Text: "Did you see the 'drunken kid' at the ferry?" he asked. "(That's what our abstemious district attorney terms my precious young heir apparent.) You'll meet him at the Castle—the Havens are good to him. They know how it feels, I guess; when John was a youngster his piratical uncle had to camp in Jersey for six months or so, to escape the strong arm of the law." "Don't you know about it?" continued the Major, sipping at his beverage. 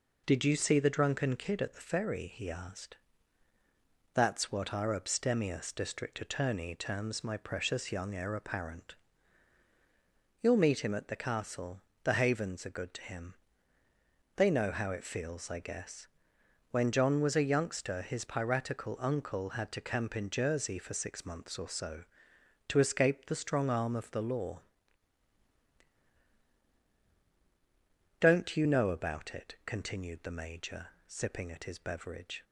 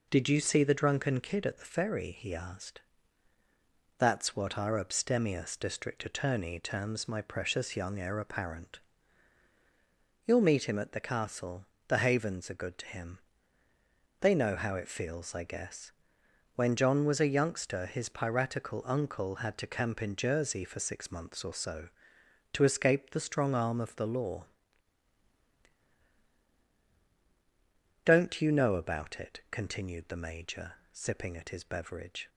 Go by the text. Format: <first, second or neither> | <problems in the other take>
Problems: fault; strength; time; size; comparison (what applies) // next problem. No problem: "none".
neither | none